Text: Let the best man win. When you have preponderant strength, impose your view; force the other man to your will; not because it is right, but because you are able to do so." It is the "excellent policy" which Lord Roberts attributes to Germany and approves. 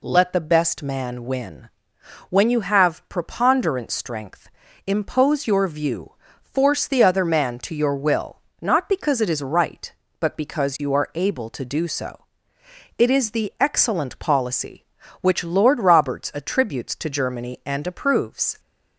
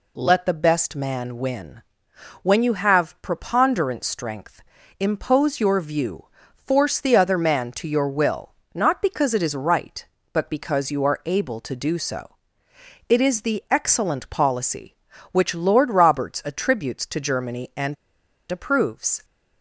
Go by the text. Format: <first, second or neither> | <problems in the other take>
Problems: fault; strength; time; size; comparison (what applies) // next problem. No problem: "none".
first | pauses between "and" and "approves"; noticeable; at 17.9 s; 0.57 s long